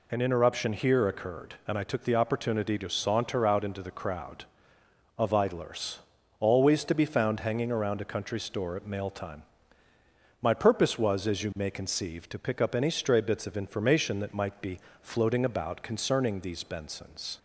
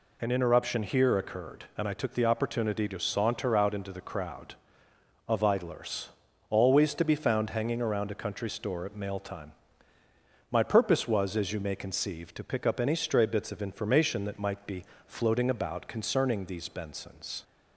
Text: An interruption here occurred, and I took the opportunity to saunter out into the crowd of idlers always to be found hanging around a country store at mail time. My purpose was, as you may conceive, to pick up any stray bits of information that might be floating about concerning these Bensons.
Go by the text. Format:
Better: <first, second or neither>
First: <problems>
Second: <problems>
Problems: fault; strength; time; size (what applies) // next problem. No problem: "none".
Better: neither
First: pauses between "idlers" and "always"; at 5.9 s; 0.42 s long // pauses between "be" and "floating"; slight; at 14.7 s; 0.22 s long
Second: pauses between "idlers" and "always"; at 6.0 s; 0.42 s long // pauses between "be" and "floating"; slight; at 14.8 s; 0.22 s long